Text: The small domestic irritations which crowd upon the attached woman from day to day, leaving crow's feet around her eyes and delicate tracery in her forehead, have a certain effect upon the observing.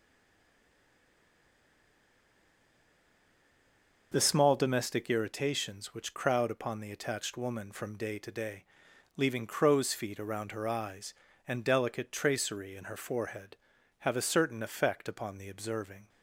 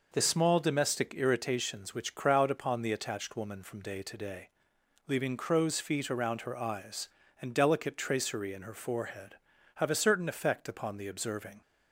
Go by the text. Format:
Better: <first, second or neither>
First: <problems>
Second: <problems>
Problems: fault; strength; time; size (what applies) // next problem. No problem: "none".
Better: second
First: stays silent before the first word; strong; until 4.1 s; 4.1 s long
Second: none